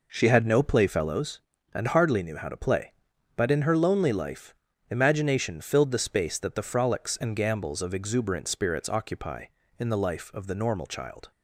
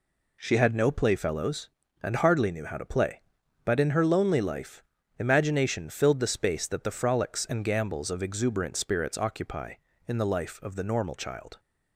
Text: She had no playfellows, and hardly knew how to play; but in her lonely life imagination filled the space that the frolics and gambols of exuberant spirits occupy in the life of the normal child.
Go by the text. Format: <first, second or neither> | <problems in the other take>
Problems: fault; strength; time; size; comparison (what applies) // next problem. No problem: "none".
second | starts louder than the rest; noticeable; until 1.1 s; 4.5 dB // pauses between "life" and "imagination"; slight; at 4.5 s; 0.36 s long; slight in the second